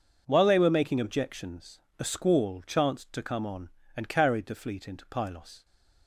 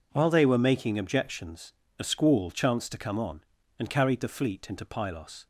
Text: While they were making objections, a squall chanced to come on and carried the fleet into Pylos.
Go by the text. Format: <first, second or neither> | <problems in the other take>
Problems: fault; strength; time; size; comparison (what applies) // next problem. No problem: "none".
neither | none